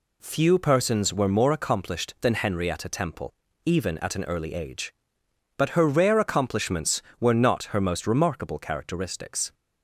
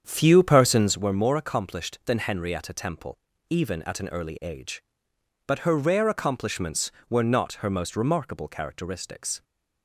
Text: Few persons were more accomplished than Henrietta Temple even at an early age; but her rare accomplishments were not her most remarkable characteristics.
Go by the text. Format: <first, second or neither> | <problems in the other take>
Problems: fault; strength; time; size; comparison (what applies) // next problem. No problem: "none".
first | starts louder than the rest; strong; until 1.0 s; 8 dB // pauses between "Temple" and "even"; slight; at 3.1 s; 0.30 s long; slight in the first